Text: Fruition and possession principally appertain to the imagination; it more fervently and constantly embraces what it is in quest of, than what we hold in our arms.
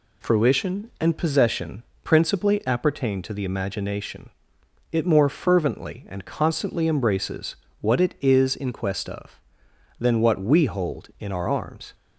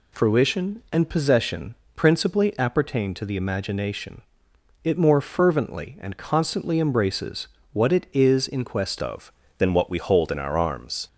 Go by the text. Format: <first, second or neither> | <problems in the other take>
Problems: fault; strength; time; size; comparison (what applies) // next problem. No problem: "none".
first | pauses between "possession" and "principally"; slight; at 1.7 s; 0.22 s long; slight in the first // pauses between "embraces" and "what"; slight; at 7.4 s; 0.24 s long; slight in the first // changes voice at "of"; from 9.0 s on; 2.0 s long